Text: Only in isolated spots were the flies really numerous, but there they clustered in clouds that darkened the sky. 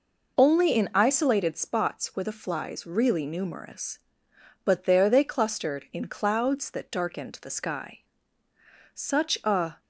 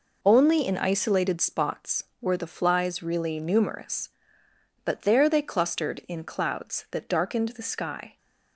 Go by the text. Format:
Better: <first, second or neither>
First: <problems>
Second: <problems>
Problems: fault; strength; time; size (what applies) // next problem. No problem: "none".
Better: second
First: goes on to say "Such a"; noticeable; from 8.9 s on; 0.88 s long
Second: none